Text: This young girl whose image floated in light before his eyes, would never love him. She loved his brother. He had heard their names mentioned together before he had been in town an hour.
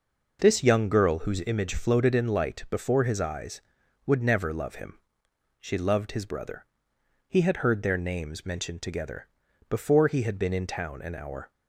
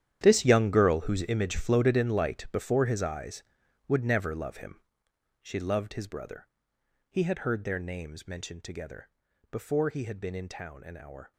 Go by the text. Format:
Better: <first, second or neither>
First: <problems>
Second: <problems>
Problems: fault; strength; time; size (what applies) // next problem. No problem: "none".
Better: first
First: pauses between "together" and "before"; at 9.2 s; 0.40 s long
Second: gets quieter; strong; throughout; 16 dB // pauses between "together" and "before"; at 9.1 s; 0.40 s long